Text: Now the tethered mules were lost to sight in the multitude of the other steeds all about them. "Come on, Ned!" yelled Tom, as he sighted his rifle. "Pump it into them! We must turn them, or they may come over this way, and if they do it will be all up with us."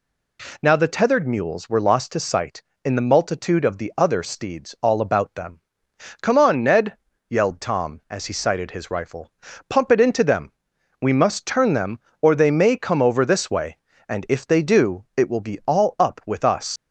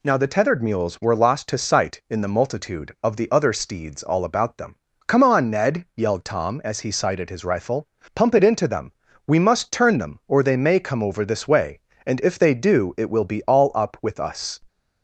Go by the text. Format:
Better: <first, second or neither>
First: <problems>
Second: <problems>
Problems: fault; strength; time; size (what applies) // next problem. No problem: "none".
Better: second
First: leaves "us" unfinished; at 16.7 s; 105 ms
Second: none